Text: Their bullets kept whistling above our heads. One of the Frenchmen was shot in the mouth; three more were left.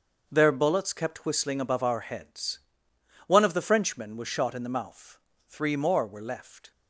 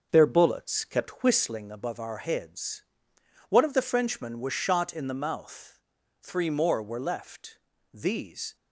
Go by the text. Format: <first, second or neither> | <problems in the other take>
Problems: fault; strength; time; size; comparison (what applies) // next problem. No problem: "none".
first | starts louder than the rest; until 1.1 s; 6.5 dB; also in the first // goes on to say "These"; noticeable; from 7.9 s on; 0.62 s long